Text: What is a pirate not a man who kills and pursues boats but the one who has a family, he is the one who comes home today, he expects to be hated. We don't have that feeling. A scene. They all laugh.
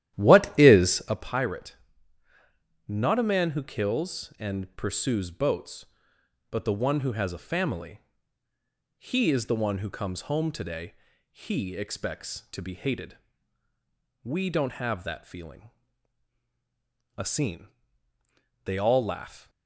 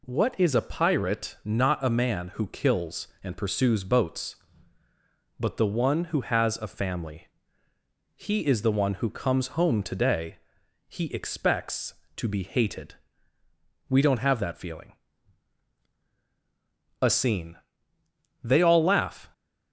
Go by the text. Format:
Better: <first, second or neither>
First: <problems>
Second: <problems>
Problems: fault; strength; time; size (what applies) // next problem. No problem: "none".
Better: second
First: starts louder than the rest; strong; until 1.3 s; 12.5 dB // pauses between "pirate" and "not"; at 1.7 s; 1.1 s long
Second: none